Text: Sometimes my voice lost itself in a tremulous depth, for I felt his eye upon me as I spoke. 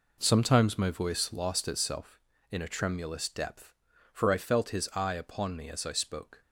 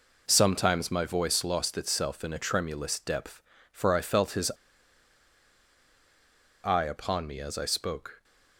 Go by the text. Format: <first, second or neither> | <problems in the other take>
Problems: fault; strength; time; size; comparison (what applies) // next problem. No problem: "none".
first | pauses between "his" and "eye"; strong; at 4.4 s; 2.1 s long